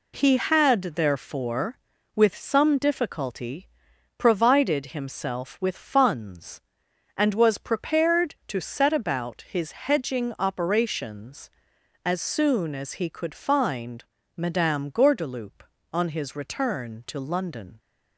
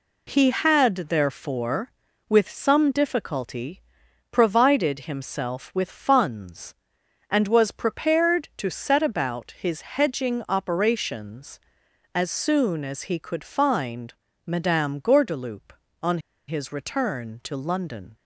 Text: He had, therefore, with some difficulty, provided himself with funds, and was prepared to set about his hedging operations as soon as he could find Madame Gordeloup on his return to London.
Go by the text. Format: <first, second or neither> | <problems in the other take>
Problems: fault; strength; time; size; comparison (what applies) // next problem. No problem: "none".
first | pauses between "find" and "Madame"; slight; at 14.1 s; 0.32 s long; slight in the first // pauses between "on" and "his"; slight; at 16.1 s; 0.29 s long